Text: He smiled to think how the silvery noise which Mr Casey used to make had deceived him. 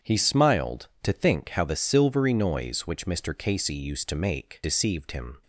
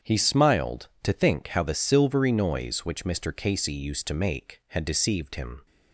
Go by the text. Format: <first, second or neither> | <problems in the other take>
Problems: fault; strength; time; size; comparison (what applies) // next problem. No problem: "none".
second | starts louder than the rest; strong; until 1.1 s; 8 dB; strong in the second // skips "had"; at 4.6 s